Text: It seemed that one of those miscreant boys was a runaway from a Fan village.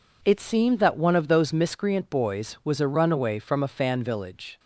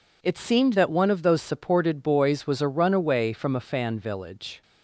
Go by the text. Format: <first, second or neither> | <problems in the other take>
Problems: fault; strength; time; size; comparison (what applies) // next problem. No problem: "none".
first | says "supported" for "miscreant"; at 1.4 s